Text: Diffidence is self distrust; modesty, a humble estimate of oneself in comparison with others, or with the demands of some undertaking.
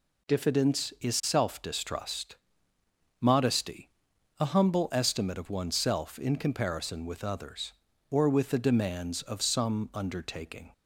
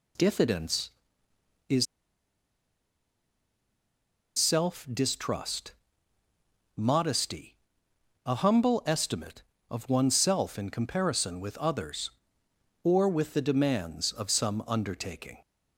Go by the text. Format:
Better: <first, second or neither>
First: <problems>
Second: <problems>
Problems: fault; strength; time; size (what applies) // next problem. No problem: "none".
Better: first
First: none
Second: pauses between "is" and "self"; strong; at 1.8 s; 2.5 s long